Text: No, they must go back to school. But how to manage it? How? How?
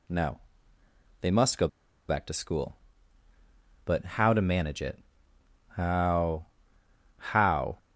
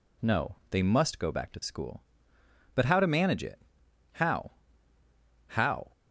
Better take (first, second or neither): second